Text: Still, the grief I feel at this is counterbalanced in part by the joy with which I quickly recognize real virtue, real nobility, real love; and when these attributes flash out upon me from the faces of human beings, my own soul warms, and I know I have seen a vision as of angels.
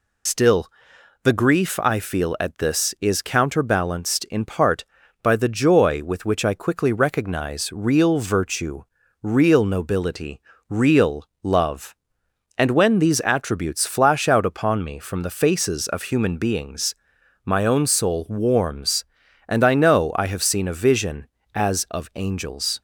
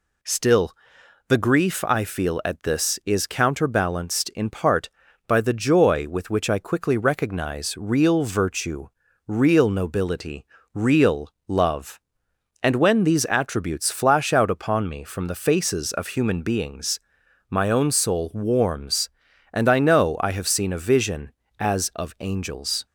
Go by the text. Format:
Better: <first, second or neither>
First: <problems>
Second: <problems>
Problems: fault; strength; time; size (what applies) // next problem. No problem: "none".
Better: second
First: loses the start of "Still"; at 0.2 s; 70 ms // pauses between "real" and "love"; slight; at 11.2 s; 0.16 s long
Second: pauses between "real" and "love"; slight; at 11.3 s; 0.16 s long